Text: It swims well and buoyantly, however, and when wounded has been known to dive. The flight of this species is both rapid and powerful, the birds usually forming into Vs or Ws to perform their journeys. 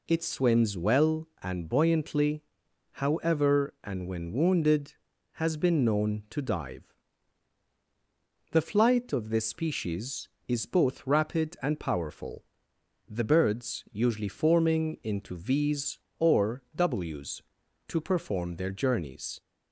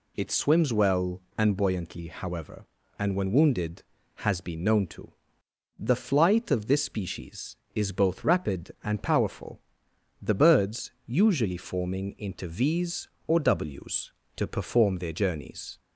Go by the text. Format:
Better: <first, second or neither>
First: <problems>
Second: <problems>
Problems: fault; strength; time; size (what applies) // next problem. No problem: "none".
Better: first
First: none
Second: skips "dive"; at 5.4 s // pauses between "birds" and "usually"; slight; at 10.9 s; 0.16 s long